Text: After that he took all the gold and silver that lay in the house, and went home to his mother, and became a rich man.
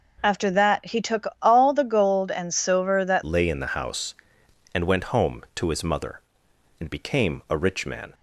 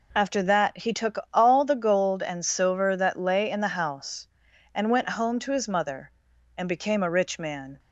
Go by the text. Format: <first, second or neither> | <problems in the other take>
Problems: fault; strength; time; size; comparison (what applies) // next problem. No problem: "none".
second | changes voice at "lay"; from 3.2 s on; 4.9 s long